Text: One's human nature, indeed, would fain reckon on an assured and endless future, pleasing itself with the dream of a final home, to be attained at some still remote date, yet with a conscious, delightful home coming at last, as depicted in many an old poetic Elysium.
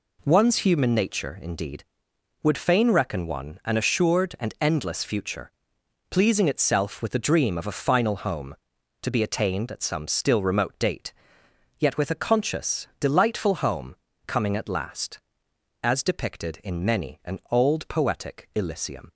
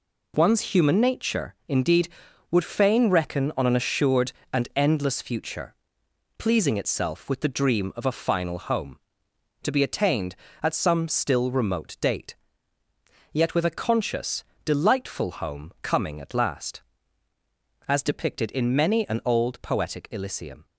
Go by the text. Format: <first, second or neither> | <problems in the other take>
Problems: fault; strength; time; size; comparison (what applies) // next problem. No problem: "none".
second | says "one" for "on"; at 3.2 s // pauses between "home" and "coming"; slight; at 13.9 s; 0.30 s long